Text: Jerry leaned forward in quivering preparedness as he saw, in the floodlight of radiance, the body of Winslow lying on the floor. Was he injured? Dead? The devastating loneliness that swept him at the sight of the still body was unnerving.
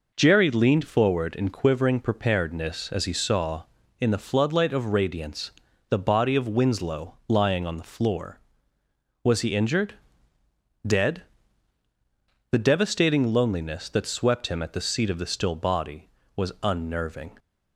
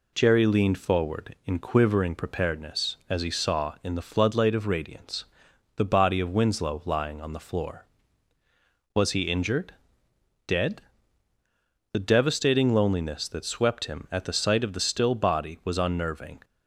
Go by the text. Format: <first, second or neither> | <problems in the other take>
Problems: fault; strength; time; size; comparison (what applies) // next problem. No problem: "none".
second | says "seat" for "sight"; at 14.8 s